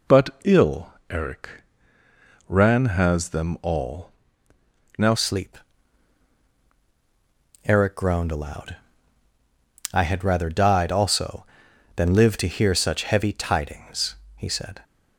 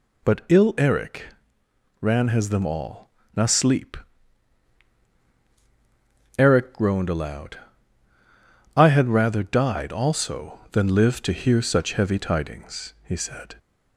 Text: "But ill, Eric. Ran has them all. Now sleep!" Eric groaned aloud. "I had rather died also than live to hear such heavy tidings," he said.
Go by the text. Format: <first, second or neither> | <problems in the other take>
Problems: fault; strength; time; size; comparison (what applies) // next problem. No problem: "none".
second | pauses between "But" and "ill"; slight; at 0.2 s; 0.16 s long // changes voice at "sleep"; from 5.1 s on; 9.7 s long